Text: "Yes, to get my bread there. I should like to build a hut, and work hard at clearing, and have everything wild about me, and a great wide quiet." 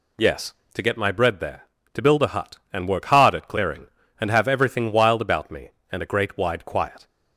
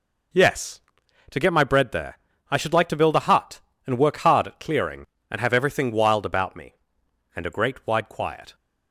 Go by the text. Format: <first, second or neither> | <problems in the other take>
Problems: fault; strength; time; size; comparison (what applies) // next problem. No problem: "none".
second | skips "I should like"; at 1.8 s